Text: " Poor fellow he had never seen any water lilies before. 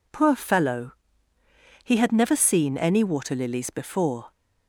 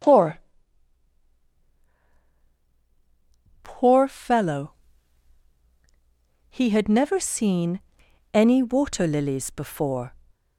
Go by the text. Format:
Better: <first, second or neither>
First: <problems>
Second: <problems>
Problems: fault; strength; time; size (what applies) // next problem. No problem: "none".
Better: first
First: pauses between "fellow" and "he"; noticeable; at 0.9 s; 0.92 s long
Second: says "Poor" twice; at 3.6 s // pauses between "fellow" and "he"; strong; at 4.7 s; 1.7 s long // pauses between "seen" and "any"; noticeable; at 7.7 s; 0.54 s long